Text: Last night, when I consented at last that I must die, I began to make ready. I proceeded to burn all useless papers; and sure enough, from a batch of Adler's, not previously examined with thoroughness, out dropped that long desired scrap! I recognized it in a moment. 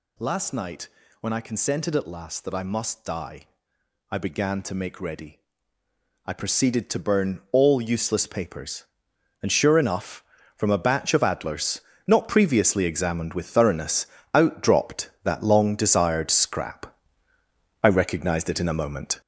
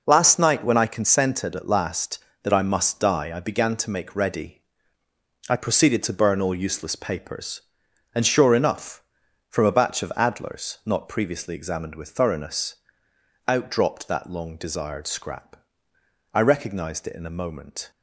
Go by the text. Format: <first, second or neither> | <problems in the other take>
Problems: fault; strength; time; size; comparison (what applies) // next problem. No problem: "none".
second | gets louder; throughout; 6.5 dB